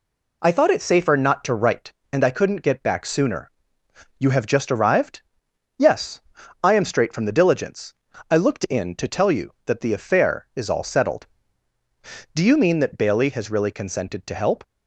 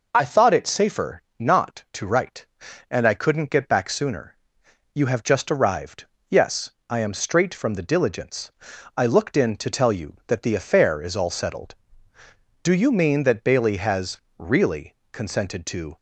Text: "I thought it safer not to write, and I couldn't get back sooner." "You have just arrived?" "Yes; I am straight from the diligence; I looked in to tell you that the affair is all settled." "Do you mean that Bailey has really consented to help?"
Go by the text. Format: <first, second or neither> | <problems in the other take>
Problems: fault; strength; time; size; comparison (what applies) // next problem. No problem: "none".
first | pauses between "safer" and "not"; slight; at 1.2 s; 0.16 s long // pauses between "has" and "really"; slight; at 14.1 s; 0.20 s long // pauses between "really" and "consented"; slight; at 14.9 s; 0.18 s long // stops before "help"; at 15.9 s